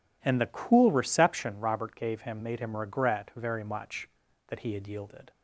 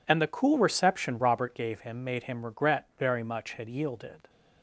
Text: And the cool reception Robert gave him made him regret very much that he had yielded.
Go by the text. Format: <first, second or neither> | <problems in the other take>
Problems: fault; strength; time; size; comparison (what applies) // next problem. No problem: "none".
first | skips "that he"; at 3.5 s